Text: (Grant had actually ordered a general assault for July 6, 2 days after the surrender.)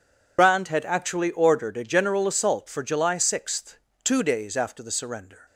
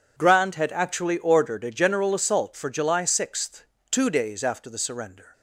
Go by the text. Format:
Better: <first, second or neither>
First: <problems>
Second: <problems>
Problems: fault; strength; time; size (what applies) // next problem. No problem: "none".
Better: second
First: loses the start of "Grant"; at 0.3 s; 75 ms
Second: none